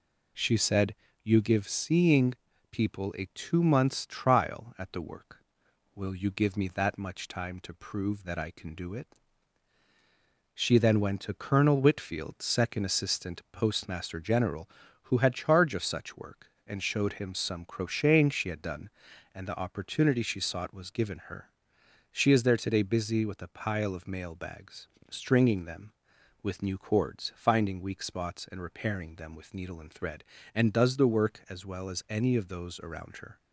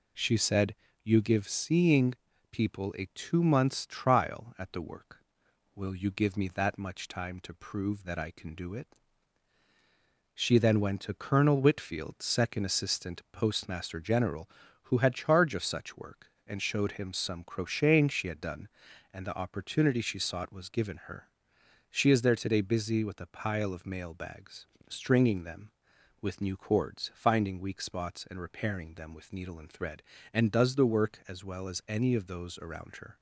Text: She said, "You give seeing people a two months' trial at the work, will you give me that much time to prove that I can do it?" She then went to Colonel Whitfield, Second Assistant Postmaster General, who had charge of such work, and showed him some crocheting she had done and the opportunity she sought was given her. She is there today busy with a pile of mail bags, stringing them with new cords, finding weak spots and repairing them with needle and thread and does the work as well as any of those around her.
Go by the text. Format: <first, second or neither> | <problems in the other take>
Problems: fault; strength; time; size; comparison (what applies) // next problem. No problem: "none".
neither | pauses between "seeing" and "people"; slight; the same in both